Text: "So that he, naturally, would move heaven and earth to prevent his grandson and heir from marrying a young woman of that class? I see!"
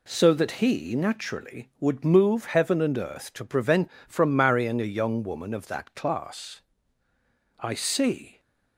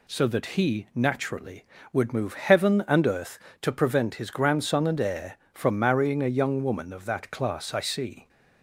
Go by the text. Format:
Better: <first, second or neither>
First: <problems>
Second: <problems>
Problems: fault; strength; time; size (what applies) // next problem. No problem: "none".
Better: second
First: skips "his grandson and heir"; at 3.9 s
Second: none